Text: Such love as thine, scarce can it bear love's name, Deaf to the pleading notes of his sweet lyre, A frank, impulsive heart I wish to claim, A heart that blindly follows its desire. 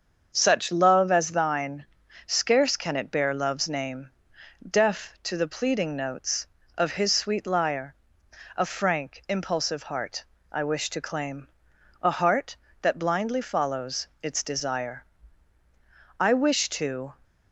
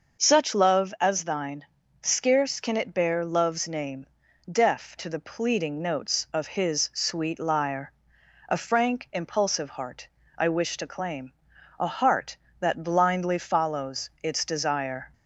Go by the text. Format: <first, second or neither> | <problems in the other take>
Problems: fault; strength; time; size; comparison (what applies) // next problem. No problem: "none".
second | starts louder than the rest; until 1.3 s; 7 dB; noticeable in the second // pauses between "heart" and "I"; slight; at 10.2 s; 0.26 s long; slight in the second // pauses between "follows" and "its"; slight; at 14.0 s; 0.16 s long // goes on to say "I wish to"; noticeable; from 16.1 s on; 0.94 s long